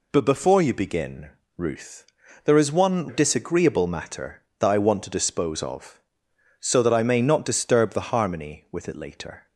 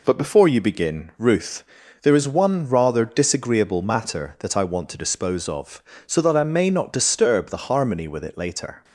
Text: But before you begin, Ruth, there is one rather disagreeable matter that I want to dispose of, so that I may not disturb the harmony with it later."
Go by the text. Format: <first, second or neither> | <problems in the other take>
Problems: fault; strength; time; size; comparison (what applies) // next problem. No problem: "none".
second | skips "rather"; at 3.0 s